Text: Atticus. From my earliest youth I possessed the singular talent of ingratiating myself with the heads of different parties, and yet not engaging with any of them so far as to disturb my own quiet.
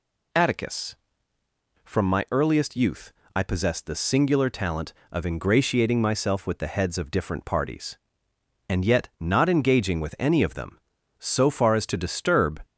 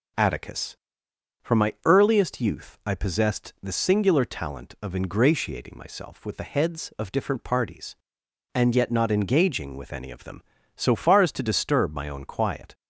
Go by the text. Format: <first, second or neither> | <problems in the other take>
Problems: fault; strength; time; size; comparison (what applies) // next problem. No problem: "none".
second | pauses between "youth" and "I"; slight; at 3.1 s; 0.24 s long // stops before "my own quiet"; at 12.6 s